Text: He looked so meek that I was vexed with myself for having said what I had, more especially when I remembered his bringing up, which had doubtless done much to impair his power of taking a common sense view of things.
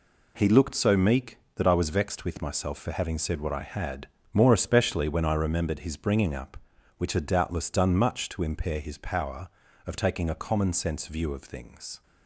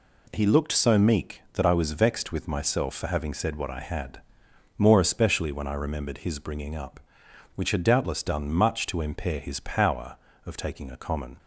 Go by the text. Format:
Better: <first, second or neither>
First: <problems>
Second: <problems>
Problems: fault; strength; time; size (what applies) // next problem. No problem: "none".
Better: first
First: none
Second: stops before "sense view of things"; at 11.3 s